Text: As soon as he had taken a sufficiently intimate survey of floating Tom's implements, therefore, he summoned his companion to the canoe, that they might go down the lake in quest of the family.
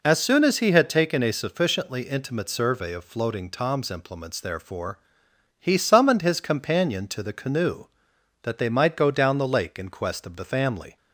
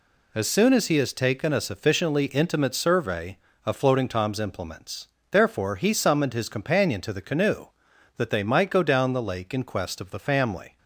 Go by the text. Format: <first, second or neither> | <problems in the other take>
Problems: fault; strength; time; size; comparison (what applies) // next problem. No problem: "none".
first | says "has" for "had"; at 0.9 s